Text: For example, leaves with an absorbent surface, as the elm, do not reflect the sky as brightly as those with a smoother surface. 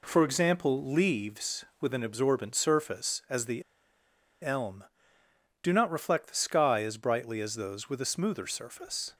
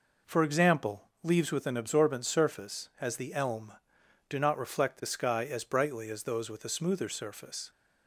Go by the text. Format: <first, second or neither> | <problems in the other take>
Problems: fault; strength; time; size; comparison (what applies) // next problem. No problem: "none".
second | pauses between "the" and "elm"; noticeable; at 3.6 s; 0.80 s long